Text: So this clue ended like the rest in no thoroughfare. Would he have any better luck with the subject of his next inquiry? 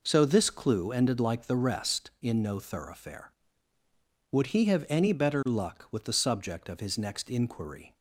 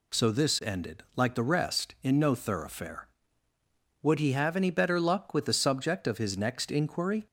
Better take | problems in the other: first | skips "clue"; at 0.5 s

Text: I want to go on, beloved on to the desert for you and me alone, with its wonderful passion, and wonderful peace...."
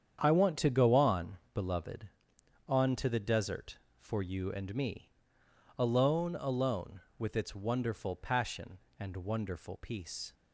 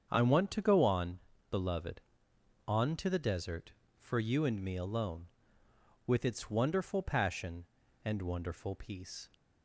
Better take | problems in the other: second | starts louder than the rest; strong; until 1.2 s; 8.5 dB; strong in the second // pauses between "me" and "alone"; noticeable; at 5.0 s; 0.70 s long // says "alone" twice; at 6.3 s

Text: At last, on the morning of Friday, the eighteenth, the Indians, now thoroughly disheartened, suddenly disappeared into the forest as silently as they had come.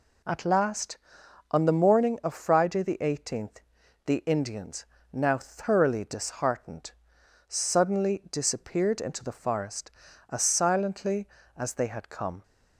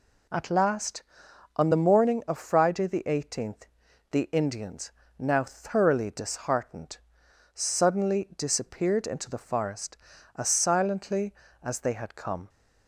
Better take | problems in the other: neither | none

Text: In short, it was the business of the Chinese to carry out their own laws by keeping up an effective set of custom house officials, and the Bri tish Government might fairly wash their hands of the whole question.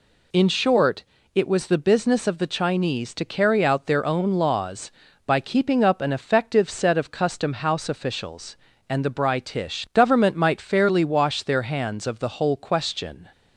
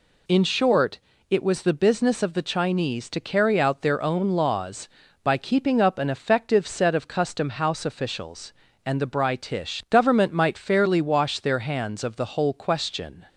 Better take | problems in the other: neither | none

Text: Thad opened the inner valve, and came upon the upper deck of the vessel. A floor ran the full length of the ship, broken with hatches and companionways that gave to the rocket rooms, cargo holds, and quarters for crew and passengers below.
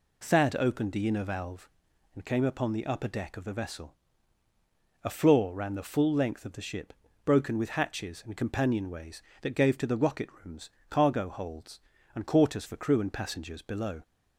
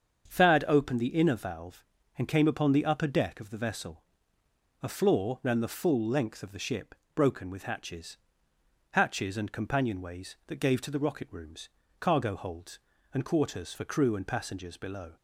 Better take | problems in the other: first | starts louder than the rest; strong; until 1.3 s; 7 dB // says "hatches" twice; at 8.9 s

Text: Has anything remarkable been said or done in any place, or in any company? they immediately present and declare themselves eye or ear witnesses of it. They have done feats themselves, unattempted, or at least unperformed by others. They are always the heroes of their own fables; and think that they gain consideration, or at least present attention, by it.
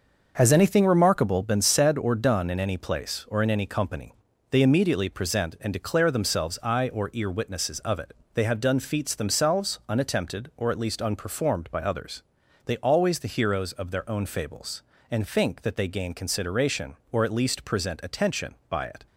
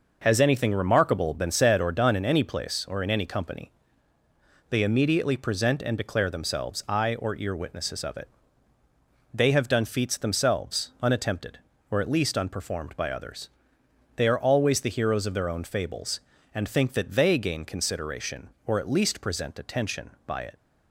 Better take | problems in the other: second | starts louder than the rest; noticeable; until 1.3 s; 6 dB // skips "are"; at 12.7 s

